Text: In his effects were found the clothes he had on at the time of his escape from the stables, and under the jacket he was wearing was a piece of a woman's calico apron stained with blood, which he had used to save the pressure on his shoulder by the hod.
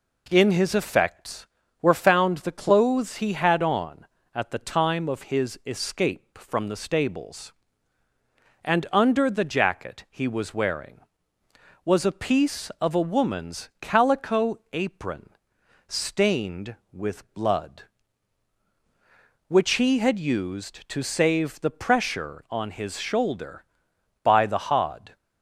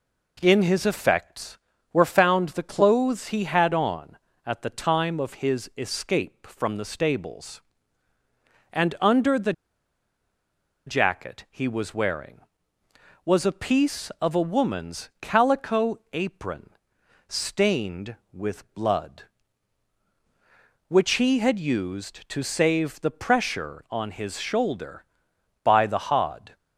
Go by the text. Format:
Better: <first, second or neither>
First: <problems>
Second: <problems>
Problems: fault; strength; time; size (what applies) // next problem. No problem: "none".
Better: first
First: pauses between "apron" and "stained"; noticeable; at 15.2 s; 0.58 s long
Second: pauses between "the" and "jacket"; strong; at 9.5 s; 1.3 s long // pauses between "apron" and "stained"; noticeable; at 16.6 s; 0.58 s long